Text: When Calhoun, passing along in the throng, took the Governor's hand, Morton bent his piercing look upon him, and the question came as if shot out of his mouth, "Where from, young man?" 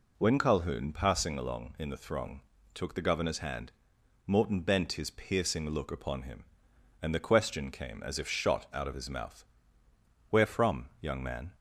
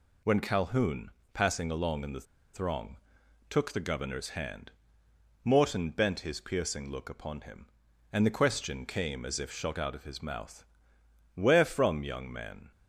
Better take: first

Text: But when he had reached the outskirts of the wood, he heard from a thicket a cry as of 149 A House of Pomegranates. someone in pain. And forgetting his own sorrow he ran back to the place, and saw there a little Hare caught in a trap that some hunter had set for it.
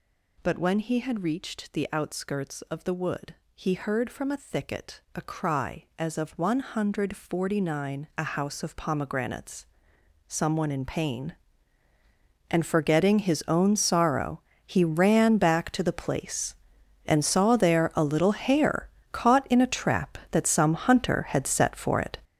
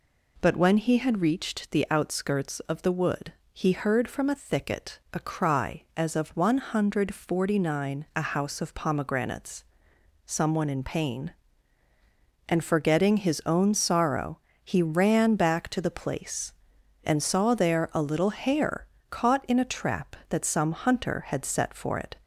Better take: second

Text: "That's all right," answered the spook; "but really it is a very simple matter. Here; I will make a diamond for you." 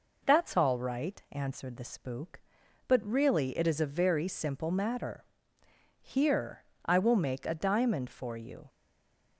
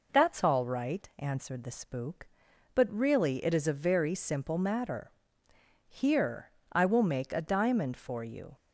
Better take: second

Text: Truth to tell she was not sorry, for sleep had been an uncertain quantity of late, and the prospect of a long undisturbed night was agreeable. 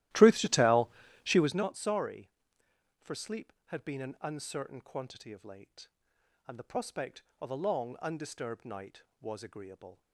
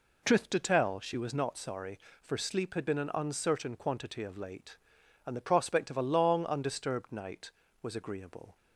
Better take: second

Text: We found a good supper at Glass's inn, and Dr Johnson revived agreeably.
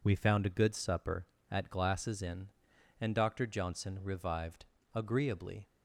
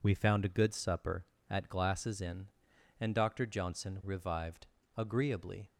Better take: neither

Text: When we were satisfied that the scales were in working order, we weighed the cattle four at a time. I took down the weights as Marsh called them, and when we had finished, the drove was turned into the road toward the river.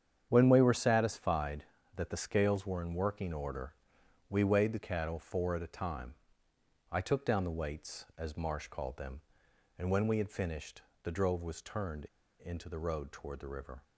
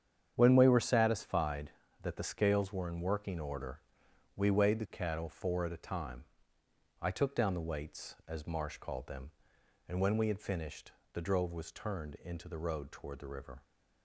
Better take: second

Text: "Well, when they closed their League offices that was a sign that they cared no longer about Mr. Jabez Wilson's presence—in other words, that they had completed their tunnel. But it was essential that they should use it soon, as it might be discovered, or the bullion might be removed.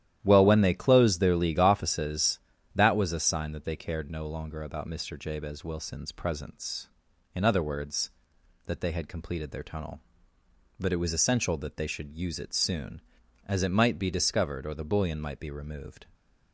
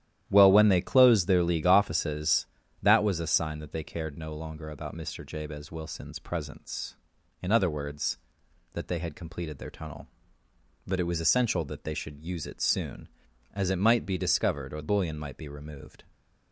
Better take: first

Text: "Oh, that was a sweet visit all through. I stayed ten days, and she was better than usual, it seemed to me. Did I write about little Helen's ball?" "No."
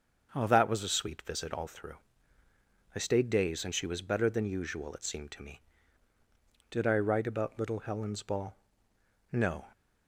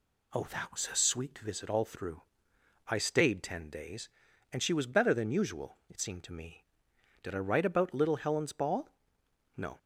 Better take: second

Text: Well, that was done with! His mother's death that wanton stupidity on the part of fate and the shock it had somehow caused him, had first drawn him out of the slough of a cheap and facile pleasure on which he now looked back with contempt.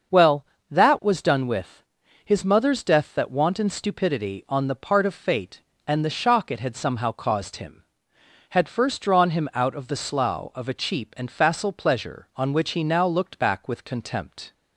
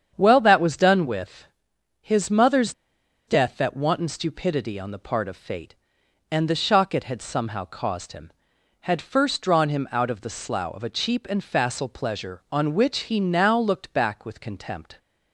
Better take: first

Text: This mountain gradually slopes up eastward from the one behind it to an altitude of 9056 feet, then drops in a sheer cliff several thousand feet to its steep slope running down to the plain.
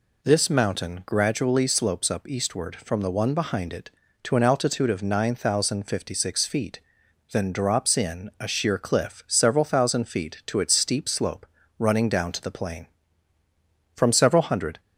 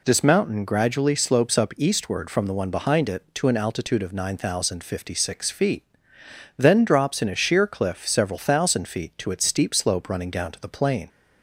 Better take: second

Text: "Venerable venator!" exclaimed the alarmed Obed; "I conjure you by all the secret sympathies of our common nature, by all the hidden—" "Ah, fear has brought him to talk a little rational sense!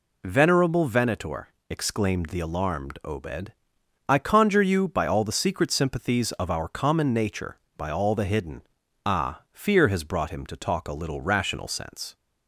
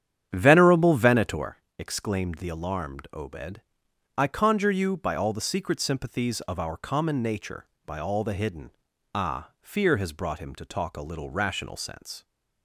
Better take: first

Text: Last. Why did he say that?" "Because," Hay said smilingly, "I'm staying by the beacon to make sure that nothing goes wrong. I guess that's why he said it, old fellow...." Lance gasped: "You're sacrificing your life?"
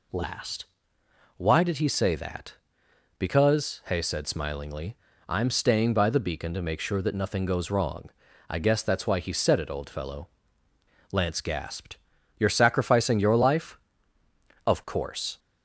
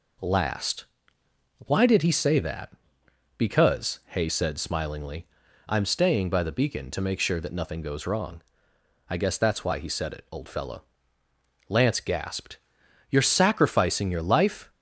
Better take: second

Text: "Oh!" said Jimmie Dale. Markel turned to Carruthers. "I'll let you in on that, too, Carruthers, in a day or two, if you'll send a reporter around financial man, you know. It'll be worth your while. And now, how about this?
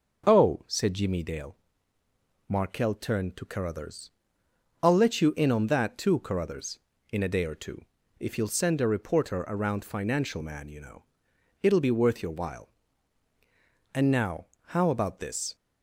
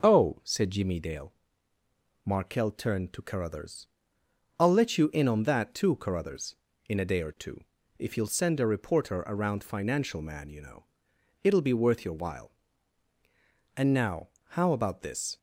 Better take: neither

